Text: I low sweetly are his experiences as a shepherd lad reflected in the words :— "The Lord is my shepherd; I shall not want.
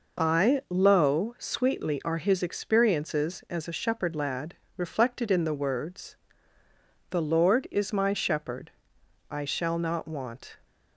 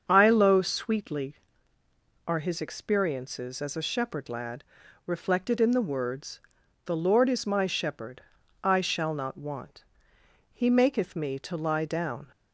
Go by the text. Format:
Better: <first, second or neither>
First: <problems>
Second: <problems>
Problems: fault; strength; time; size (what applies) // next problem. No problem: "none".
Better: first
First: pauses between "lad" and "reflected"; slight; at 4.5 s; 0.22 s long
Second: starts louder than the rest; until 1.0 s; 7 dB // pauses between "lad" and "reflected"; at 4.6 s; 0.42 s long // goes on to say "He maketh me to lie down"; strong; from 10.5 s on; 1.7 s long